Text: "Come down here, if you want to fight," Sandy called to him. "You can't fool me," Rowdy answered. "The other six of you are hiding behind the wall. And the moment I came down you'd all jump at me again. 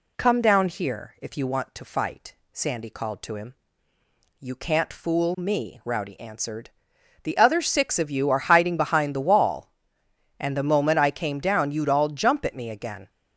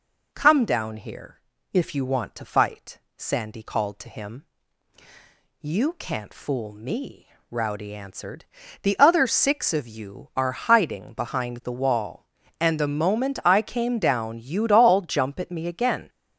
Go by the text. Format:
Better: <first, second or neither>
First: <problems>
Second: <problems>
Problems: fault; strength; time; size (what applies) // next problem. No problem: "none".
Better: neither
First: none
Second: none